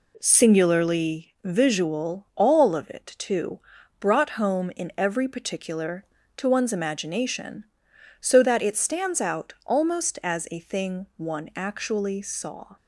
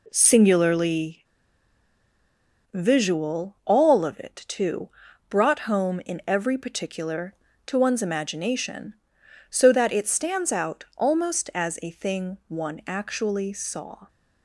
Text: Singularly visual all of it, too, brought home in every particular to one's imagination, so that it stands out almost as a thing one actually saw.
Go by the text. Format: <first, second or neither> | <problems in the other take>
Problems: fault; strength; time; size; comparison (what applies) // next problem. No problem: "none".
first | pauses between "Singularly" and "visual"; strong; at 1.2 s; 1.4 s long